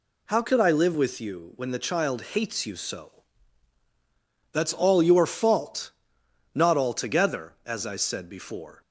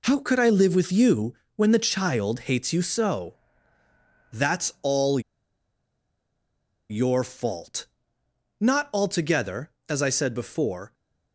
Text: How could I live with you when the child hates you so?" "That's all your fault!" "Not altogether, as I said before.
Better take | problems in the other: first | pauses between "you" and "when"; slight; at 1.3 s; 0.22 s long // pauses between "all" and "your"; strong; at 5.2 s; 1.6 s long

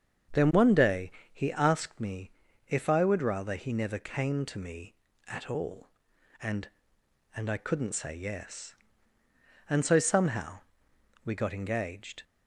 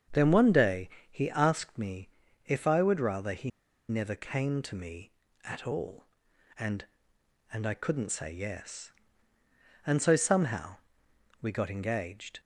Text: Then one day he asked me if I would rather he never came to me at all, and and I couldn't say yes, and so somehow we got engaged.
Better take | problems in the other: first | starts louder than the rest; until 1.3 s; 7 dB; also in the first // pauses between "day" and "he"; slight; at 0.8 s; 0.22 s long; slight in the first // pauses between "me" and "if"; at 2.0 s; 0.38 s long; also in the first // pauses between "he" and "never"; at 3.5 s; 0.39 s long // pauses between "somehow" and "we"; noticeable; at 10.7 s; 0.66 s long; noticeable in the first

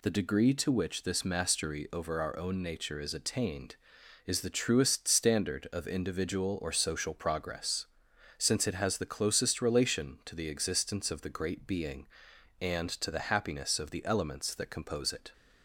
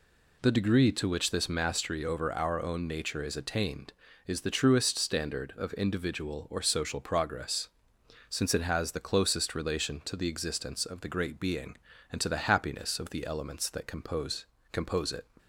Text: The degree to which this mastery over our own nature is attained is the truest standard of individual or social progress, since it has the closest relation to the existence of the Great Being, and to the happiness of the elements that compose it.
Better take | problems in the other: first | says "compose" twice; at 14.7 s

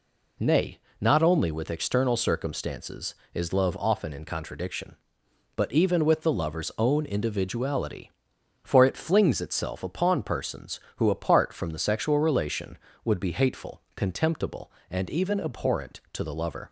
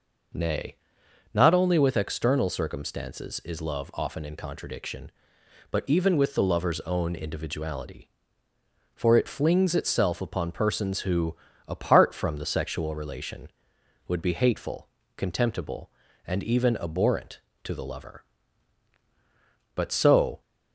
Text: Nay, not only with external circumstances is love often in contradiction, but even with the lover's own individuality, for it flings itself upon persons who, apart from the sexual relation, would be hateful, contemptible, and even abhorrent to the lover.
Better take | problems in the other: first | goes on to say "But so"; noticeable; from 19.7 s on; 0.66 s long

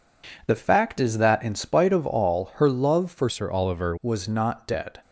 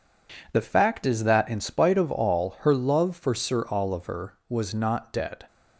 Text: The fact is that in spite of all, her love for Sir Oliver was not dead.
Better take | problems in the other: second | changes voice from "Sir" to "Oliver"; from 3.2 to 3.9 s; 0.7 s long

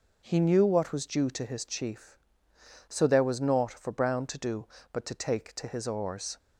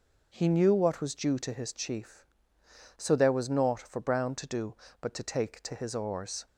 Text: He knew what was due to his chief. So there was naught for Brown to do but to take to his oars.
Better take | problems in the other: neither | none

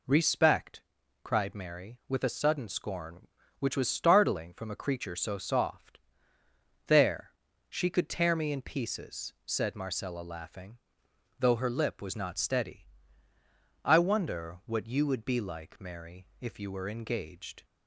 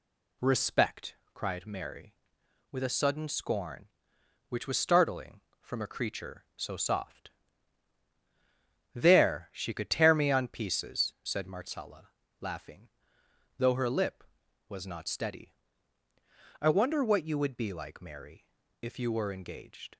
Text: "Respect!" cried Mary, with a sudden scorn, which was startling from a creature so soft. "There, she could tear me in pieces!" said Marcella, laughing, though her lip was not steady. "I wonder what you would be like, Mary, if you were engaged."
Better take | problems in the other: first | says "on" for "in"; at 10.3 s

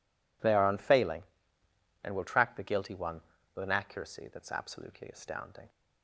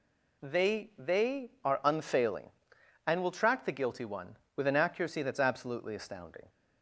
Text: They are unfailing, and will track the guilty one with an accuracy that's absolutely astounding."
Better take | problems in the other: first | says "They" twice; at 0.9 s

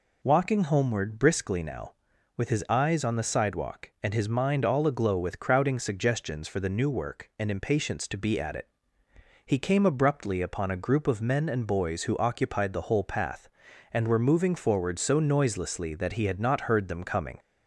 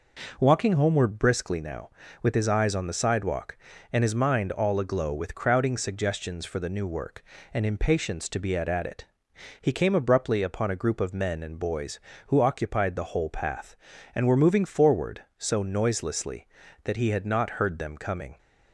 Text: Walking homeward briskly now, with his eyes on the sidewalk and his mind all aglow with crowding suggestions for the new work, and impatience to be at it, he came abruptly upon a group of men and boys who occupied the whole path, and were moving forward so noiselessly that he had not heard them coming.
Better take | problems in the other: first | says "at" twice; at 8.6 s

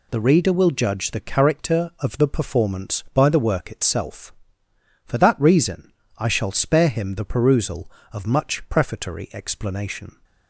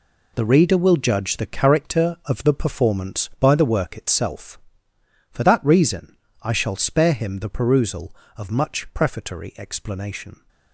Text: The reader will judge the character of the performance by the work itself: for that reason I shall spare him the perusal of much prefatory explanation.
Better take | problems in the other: first | gets quieter; strong; throughout; 11 dB // pauses between "reason" and "I"; slight; at 6.1 s; 0.24 s long; slight in the first

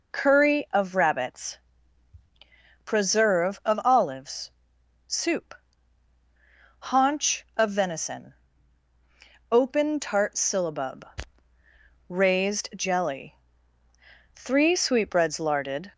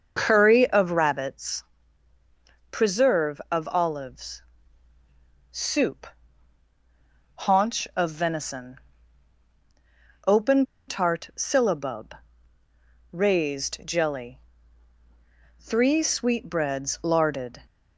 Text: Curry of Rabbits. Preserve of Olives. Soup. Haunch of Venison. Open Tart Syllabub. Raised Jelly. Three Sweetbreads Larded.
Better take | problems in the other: first | starts louder than the rest; until 1.2 s; 6.5 dB // pauses between "Open" and "Tart"; slight; at 10.6 s; 0.22 s long

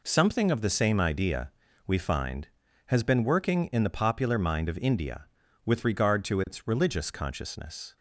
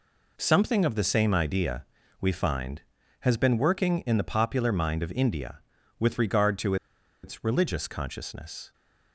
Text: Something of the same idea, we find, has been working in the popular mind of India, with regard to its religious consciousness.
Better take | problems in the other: first | pauses between "to" and "its"; noticeable; at 6.7 s; 0.48 s long

